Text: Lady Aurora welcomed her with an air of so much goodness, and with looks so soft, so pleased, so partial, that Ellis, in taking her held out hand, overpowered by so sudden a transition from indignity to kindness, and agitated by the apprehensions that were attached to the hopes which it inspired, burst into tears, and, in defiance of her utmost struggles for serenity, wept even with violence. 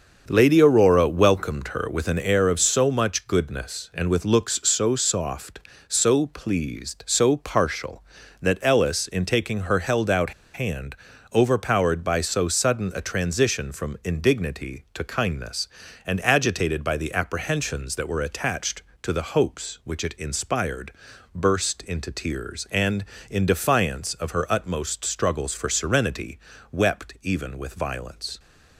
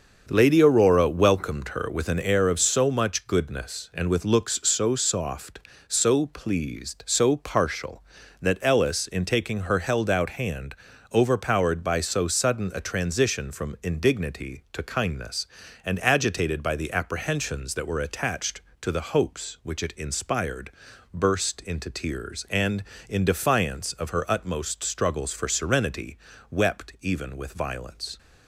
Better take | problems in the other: second | starts louder than the rest; until 1.2 s; 6.5 dB; also in the second // pauses between "out" and "hand"; slight; at 10.3 s; 0.23 s long

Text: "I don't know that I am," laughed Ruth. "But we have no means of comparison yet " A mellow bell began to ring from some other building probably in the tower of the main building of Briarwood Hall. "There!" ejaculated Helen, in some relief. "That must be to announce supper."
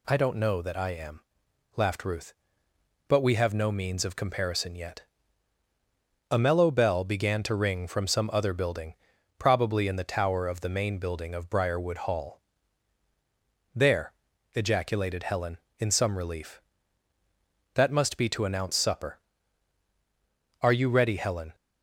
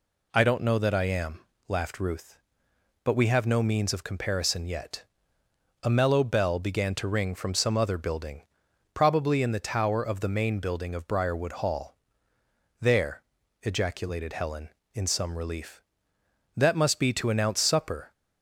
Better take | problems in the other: second | pauses between "building" and "probably"; at 8.9 s; 0.42 s long; noticeable in the second // goes on to say "Are you ready Helen"; noticeable; from 20.6 s on; 0.94 s long

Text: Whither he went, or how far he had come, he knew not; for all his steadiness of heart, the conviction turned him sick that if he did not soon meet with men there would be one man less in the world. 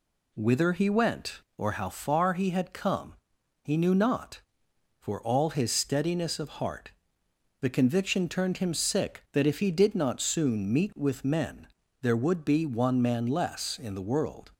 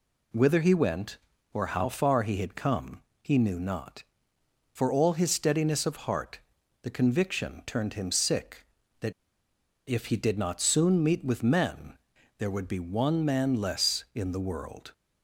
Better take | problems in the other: first | pauses between "that" and "if"; noticeable; at 9.1 s; 0.75 s long // pauses between "men" and "there"; at 11.9 s; 0.42 s long; slight in the first

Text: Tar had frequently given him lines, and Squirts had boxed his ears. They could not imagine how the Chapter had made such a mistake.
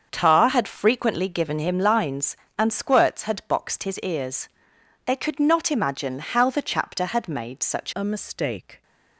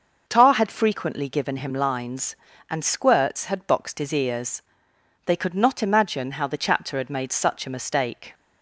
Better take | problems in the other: second | starts louder than the rest; until 1.1 s; 7 dB // changes voice at "a"; from 7.9 s on; 0.9 s long

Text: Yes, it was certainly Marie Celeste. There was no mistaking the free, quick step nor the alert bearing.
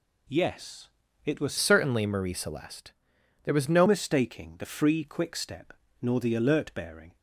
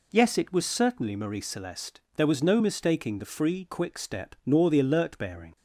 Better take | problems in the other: second | changes voice from "certainly" to "no"; from 1.5 to 3.8 s; 2.3 s long // pauses between "step" and "nor"; slight; at 5.7 s; 0.30 s long

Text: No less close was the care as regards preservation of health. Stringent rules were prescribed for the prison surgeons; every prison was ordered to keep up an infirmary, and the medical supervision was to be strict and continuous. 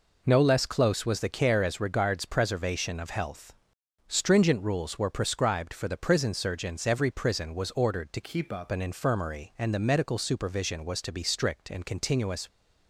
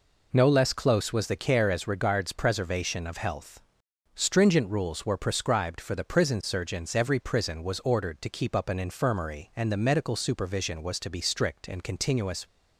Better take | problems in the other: second | changes voice from "keep" to "up"; from 8.2 to 8.7 s; 0.5 s long

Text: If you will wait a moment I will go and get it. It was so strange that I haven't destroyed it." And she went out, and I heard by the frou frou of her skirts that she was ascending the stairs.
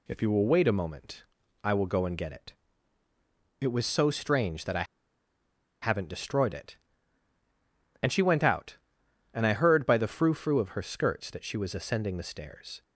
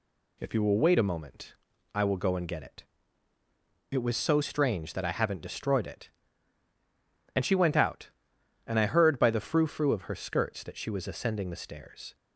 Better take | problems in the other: second | pauses between "moment" and "I"; at 1.2 s; 0.40 s long; also in the second // pauses between "I" and "haven't"; noticeable; at 4.8 s; 0.97 s long

